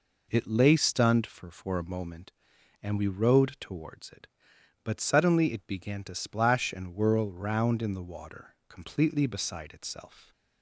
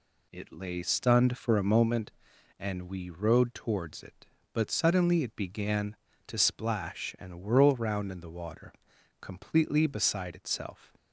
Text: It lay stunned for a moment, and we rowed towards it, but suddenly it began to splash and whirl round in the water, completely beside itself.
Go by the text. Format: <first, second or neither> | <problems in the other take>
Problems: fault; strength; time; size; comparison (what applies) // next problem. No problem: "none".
second | says "for" twice; at 1.4 s